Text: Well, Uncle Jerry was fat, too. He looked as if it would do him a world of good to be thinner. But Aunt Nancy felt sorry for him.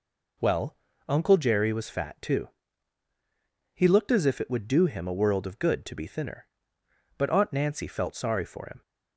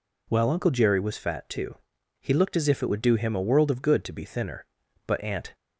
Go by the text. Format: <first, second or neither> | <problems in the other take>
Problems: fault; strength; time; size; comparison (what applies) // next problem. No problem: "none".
first | stops before "Nancy felt sorry for him"; at 5.5 s